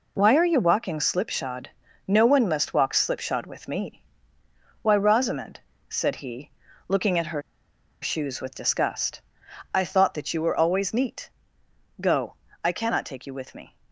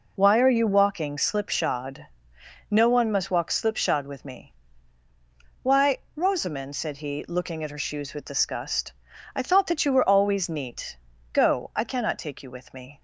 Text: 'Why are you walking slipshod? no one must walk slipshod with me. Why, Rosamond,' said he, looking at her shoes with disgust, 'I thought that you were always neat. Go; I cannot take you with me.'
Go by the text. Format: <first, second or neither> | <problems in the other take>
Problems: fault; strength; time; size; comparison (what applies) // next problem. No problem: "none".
second | pauses between "her" and "shoes"; noticeable; at 7.4 s; 0.60 s long